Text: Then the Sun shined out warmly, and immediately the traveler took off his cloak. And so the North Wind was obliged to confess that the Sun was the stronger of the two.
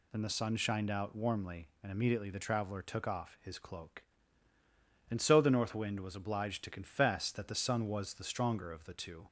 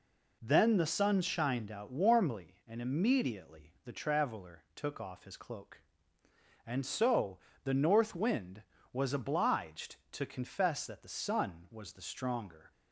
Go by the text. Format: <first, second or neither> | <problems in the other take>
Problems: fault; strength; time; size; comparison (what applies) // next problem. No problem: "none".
first | pauses between "so" and "the"; slight; at 7.3 s; 0.26 s long // stops before "of the two"; at 12.7 s